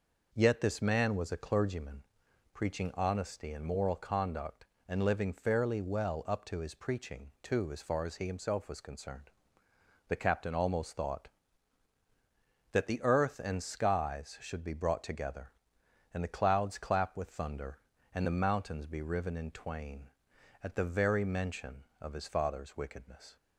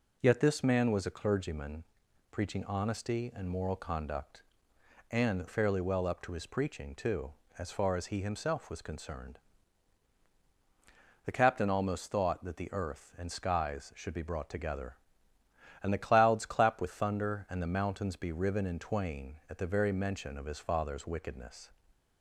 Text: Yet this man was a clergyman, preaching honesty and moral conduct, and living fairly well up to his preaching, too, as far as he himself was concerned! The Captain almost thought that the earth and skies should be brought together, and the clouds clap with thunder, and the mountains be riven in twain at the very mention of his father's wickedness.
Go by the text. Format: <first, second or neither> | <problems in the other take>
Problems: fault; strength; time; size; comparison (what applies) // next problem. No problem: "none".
first | skips "living"; at 5.4 s